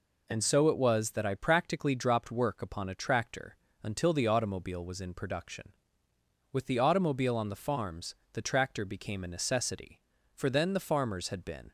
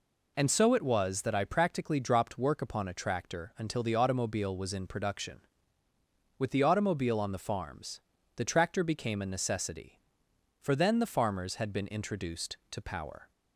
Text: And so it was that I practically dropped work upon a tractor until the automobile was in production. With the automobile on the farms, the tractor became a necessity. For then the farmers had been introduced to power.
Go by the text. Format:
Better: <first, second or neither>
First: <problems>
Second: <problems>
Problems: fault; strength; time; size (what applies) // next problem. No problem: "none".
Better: second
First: pauses between "tractor" and "until"; slight; at 3.5 s; 0.28 s long // stops before "introduced to power"; at 11.6 s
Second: none